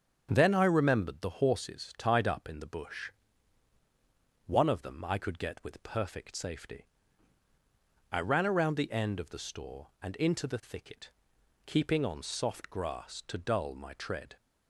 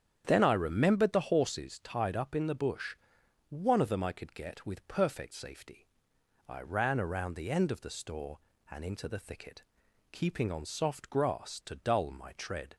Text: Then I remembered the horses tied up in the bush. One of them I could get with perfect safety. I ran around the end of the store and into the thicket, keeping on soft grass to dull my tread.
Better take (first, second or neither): neither